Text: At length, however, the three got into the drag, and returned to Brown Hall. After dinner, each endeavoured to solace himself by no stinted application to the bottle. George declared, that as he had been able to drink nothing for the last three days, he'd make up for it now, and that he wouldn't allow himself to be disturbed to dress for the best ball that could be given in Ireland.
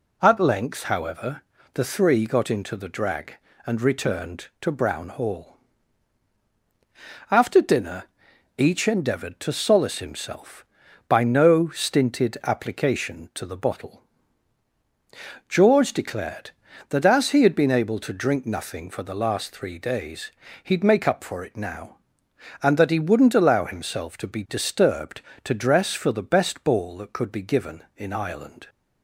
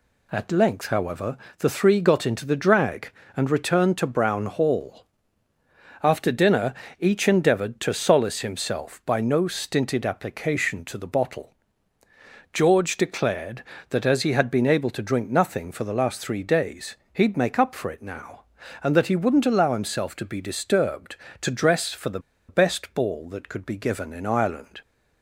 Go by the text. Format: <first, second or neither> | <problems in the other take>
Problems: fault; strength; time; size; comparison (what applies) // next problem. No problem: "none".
first | pauses between "the" and "best"; slight; at 22.1 s; 0.29 s long